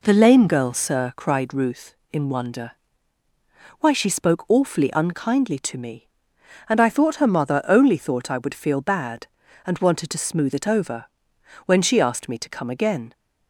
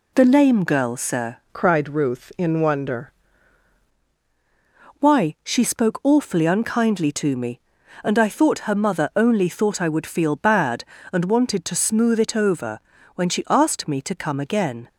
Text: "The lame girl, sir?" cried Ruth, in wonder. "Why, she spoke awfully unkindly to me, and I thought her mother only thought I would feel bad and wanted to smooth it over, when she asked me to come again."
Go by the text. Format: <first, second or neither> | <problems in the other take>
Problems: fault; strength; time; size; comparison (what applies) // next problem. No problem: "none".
first | changes voice from "cried" to "wonder"; from 1.5 to 3.1 s; 1.6 s long